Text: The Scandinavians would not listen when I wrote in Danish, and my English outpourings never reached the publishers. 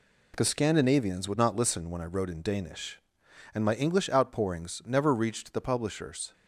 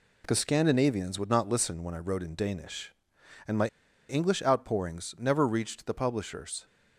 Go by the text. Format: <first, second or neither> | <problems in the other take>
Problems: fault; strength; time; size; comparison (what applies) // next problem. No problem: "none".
first | pauses between "my" and "English"; at 3.6 s; 0.41 s long